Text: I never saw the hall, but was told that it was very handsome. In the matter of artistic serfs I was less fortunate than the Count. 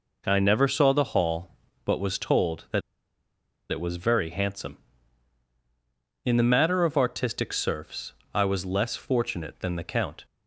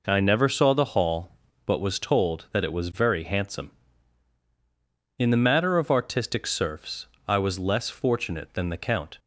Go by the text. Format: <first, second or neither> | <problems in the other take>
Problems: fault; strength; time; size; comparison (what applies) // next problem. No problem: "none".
second | pauses between "that" and "it"; noticeable; at 2.8 s; 0.89 s long // pauses between "serfs" and "I"; slight; at 8.1 s; 0.22 s long; slight in the second